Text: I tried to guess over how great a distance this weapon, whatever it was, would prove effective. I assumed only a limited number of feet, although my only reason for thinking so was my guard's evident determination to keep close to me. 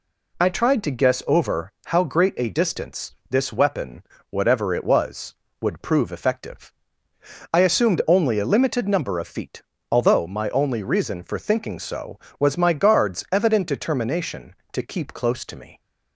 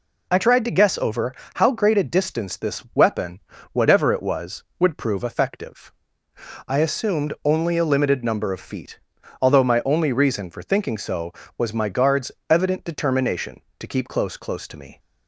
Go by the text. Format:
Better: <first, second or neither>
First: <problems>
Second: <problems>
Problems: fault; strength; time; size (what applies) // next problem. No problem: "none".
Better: first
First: none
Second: pauses between "over" and "how"; slight; at 1.3 s; 0.22 s long // pauses between "guard's" and "evident"; slight; at 12.3 s; 0.18 s long // says "close" twice; at 14.3 s